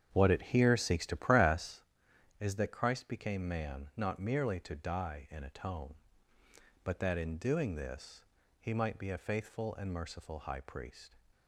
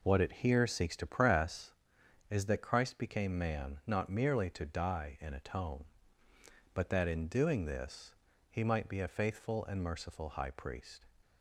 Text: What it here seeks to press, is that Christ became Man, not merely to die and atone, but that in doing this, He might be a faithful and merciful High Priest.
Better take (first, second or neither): second